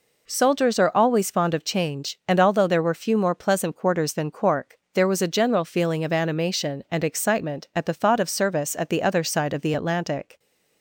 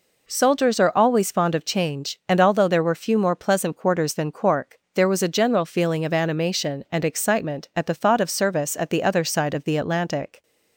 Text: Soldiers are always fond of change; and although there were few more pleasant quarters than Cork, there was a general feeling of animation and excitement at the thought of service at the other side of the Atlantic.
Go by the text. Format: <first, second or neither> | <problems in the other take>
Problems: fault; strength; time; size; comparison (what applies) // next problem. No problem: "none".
neither | none